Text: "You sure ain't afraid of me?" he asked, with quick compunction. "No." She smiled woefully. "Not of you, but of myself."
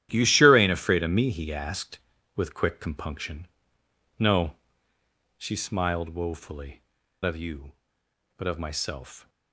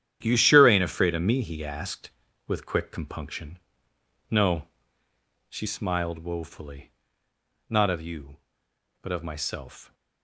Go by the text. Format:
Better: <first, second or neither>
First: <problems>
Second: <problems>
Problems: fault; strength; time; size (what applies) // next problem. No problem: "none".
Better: second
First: starts louder than the rest; strong; until 1.1 s; 11.5 dB // skips "Not"; at 7.0 s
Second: starts louder than the rest; strong; until 1.2 s; 10 dB